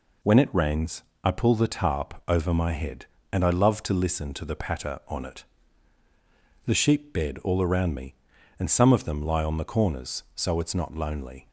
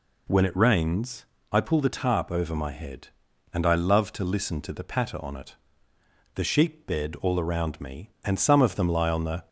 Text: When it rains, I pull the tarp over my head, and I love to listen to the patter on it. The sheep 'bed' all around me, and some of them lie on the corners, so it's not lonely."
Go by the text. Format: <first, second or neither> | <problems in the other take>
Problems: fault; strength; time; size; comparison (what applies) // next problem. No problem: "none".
first | stops before "corners so it's not lonely"; at 9.4 s